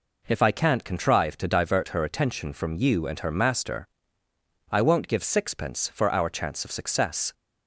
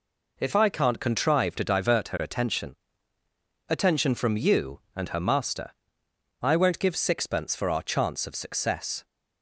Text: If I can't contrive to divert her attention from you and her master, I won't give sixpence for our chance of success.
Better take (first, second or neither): first